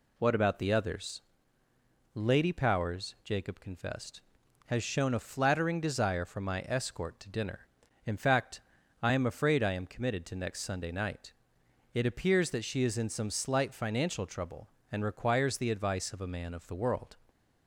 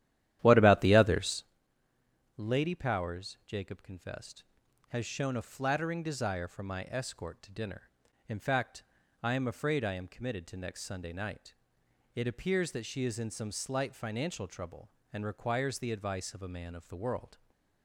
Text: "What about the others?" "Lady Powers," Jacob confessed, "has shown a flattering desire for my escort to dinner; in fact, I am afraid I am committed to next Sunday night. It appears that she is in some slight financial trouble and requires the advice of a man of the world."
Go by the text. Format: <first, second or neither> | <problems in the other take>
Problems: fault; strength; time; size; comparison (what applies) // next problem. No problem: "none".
first | starts louder than the rest; strong; until 1.5 s; 12 dB // stays silent after the last word; slight; from 17.3 s on; 0.5 s long